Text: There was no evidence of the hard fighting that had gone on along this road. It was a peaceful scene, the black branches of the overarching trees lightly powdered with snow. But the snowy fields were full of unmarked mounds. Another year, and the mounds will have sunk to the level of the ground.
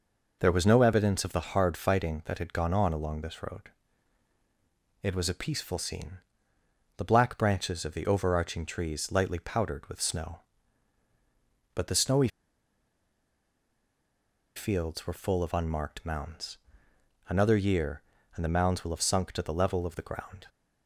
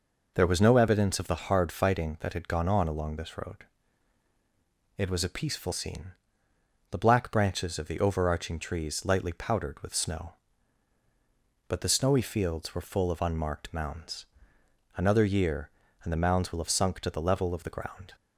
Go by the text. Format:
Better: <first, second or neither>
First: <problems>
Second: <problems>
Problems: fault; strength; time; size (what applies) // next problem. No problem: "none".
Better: second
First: pauses between "snowy" and "fields"; strong; at 12.2 s; 2.2 s long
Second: none